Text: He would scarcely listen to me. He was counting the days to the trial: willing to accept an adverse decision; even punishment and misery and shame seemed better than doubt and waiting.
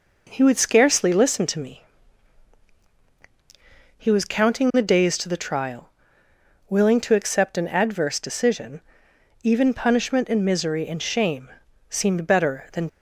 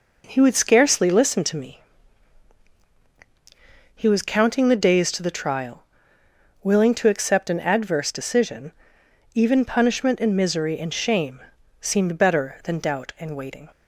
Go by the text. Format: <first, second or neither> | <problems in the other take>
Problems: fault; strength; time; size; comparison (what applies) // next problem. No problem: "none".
second | pauses between "shame" and "seemed"; at 11.4 s; 0.40 s long; also in the second // stops before "doubt and waiting"; at 12.8 s